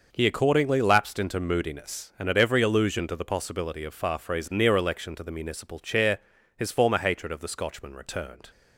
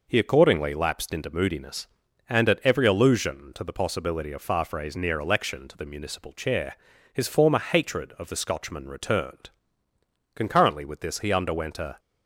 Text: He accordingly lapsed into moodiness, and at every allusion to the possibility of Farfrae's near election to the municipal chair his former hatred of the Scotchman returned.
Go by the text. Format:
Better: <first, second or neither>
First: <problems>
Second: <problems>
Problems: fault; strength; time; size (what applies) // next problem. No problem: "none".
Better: first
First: pauses between "chair" and "his"; at 6.1 s; 0.38 s long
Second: pauses between "chair" and "his"; slight; at 6.7 s; 0.36 s long // goes on to say "Concurrently with this he underwent a"; from 10.3 s on; 1.6 s long